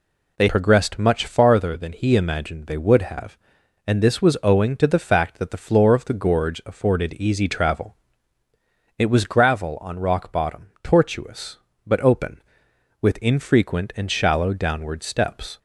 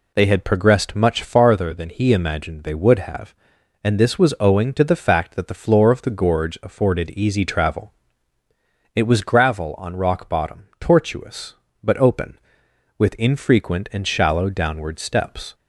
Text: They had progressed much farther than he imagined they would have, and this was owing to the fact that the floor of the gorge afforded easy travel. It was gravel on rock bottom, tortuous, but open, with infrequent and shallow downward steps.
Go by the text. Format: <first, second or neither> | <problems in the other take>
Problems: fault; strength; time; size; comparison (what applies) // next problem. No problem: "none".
second | skips "had"; at 0.4 s